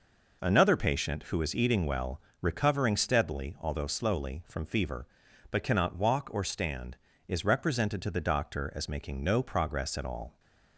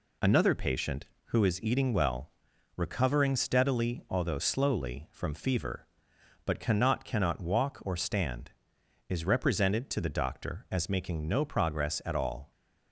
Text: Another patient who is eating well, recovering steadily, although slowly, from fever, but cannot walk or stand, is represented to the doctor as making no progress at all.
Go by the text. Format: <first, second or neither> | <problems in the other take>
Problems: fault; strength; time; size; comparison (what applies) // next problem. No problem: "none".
first | says "cannot" twice; at 7.0 s